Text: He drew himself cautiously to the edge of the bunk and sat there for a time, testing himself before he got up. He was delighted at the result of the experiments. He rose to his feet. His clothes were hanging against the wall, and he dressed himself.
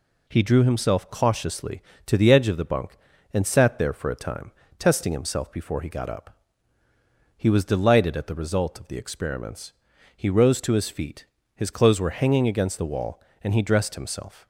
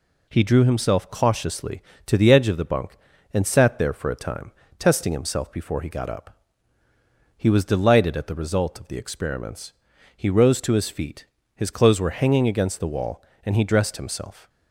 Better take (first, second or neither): neither